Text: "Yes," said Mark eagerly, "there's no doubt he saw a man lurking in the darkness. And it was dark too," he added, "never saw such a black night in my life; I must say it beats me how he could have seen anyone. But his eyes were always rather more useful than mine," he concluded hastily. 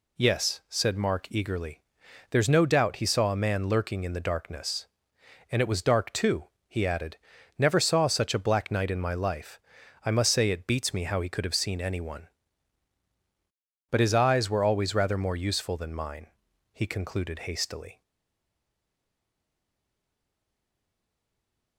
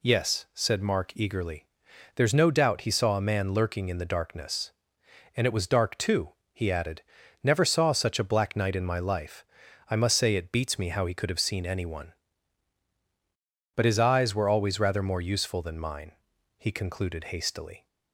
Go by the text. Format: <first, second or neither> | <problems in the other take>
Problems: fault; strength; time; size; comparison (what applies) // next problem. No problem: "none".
second | stays silent after the last word; strong; from 18.0 s on; 3.7 s long